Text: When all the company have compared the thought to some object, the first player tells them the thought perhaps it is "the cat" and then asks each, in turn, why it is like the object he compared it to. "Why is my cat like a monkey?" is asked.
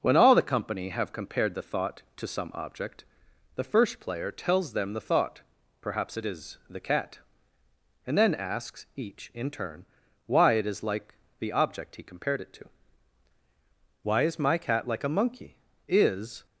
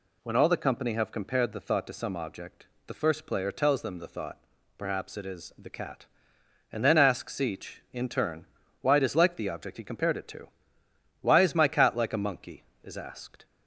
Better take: second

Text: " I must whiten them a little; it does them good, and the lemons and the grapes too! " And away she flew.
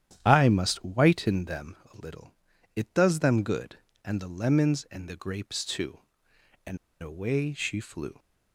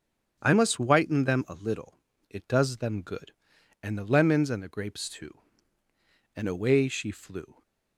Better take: second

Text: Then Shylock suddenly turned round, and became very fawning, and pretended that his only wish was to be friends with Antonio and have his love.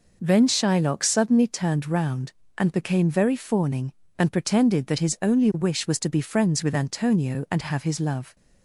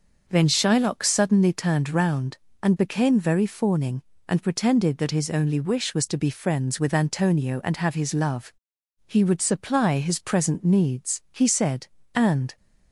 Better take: first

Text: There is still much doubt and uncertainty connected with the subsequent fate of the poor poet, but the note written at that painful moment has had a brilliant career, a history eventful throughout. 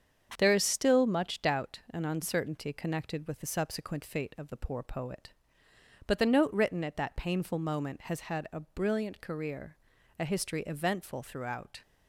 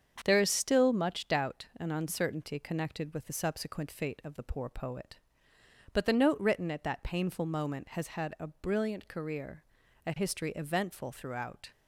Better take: neither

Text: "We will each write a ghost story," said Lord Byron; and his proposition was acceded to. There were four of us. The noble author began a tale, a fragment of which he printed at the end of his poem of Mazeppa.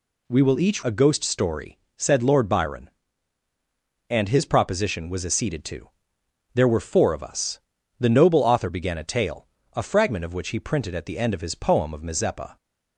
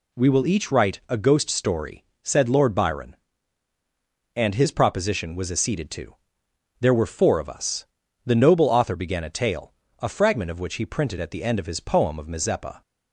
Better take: second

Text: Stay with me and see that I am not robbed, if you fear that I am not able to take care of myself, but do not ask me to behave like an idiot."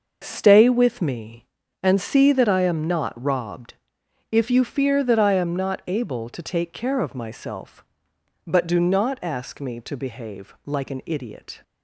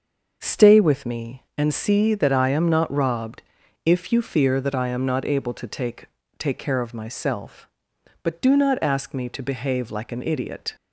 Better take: first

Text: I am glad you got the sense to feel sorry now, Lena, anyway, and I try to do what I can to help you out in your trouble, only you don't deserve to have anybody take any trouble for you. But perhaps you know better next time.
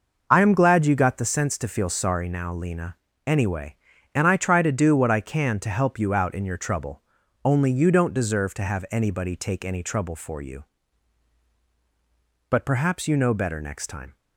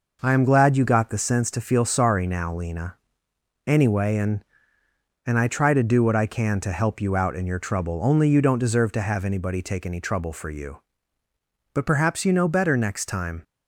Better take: first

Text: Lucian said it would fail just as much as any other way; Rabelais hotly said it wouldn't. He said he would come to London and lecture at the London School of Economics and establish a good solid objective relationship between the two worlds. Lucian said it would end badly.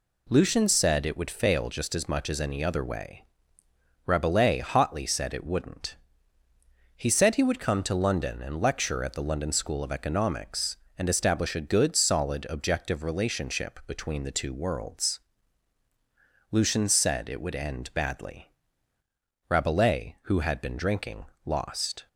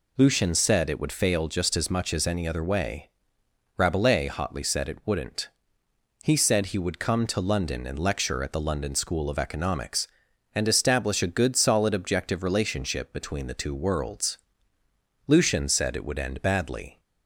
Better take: second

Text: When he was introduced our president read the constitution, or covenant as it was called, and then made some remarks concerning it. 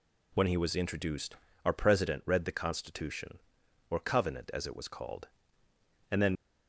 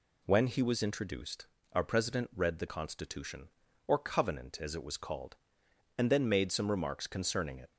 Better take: second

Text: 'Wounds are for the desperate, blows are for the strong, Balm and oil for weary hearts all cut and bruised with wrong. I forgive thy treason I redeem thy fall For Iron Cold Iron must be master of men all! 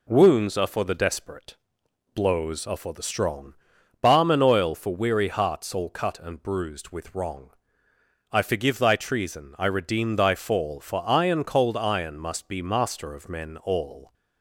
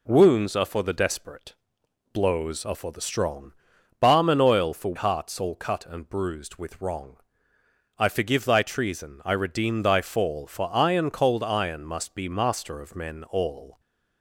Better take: first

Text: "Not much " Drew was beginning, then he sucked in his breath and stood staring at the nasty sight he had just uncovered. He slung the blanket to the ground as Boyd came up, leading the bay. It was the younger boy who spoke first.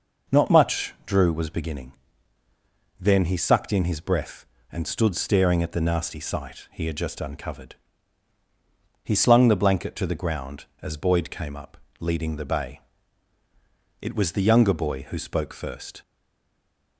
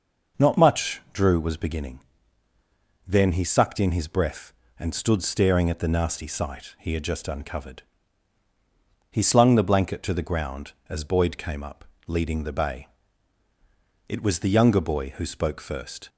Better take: second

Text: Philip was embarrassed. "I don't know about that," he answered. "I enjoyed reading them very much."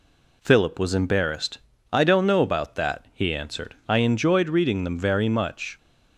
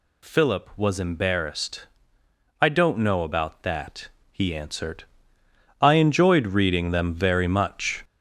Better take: first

